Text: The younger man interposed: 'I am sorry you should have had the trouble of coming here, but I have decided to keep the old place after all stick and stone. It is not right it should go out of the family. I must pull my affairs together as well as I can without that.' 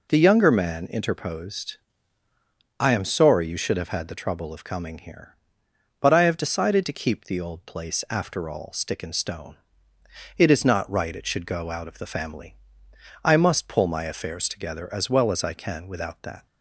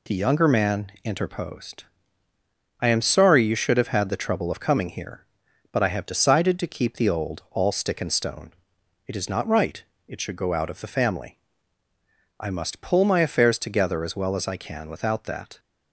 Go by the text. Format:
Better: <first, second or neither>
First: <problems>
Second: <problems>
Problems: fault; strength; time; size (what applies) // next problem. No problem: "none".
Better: first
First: none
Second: skips "place after"; at 7.4 s // pauses between "right" and "it"; slight; at 9.8 s; 0.24 s long